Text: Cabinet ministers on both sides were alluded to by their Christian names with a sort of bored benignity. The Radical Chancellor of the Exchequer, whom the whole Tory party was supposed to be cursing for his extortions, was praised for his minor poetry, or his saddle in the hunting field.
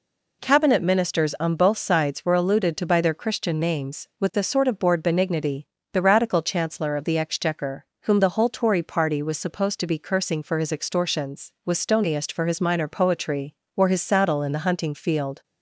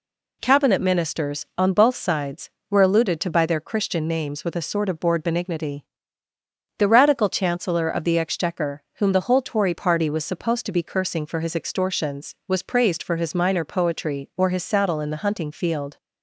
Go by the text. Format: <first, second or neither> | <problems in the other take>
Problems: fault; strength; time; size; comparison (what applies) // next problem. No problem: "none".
second | says "stoniest" for "praised"; at 11.7 s